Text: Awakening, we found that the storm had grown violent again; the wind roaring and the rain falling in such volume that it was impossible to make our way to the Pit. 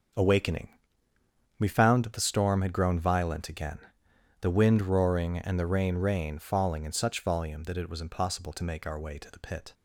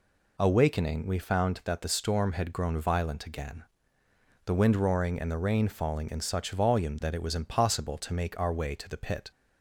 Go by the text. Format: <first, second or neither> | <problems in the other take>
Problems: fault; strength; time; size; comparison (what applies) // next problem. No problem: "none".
second | starts louder than the rest; until 2.0 s; 7 dB // says "rain" twice; at 5.9 s